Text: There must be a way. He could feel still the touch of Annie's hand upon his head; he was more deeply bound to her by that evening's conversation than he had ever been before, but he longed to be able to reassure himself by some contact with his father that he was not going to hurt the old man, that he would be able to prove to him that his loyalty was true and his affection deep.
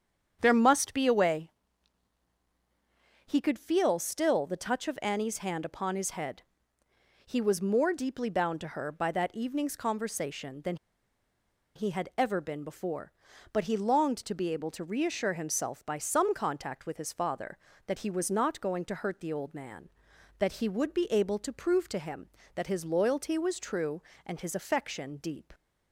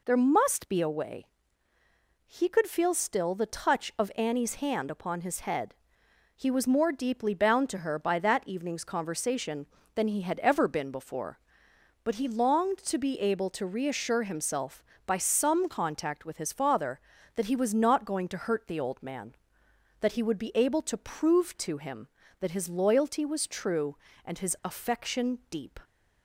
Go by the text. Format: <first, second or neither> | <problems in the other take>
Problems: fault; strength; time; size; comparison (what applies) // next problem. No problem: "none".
second | starts louder than the rest; strong; until 1.4 s; 8.5 dB // pauses between "than" and "he"; at 10.7 s; 0.99 s long